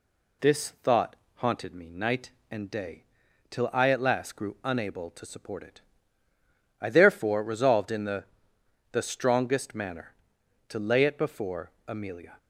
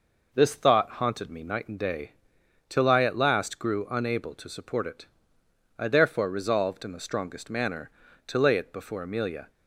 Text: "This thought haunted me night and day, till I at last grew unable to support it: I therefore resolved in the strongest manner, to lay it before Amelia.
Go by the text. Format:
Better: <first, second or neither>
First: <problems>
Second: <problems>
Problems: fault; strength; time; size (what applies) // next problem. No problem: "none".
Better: second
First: pauses between "thought" and "haunted"; slight; at 1.1 s; 0.20 s long // says "the" twice; at 8.9 s // pauses between "before" and "Amelia"; slight; at 11.7 s; 0.16 s long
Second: none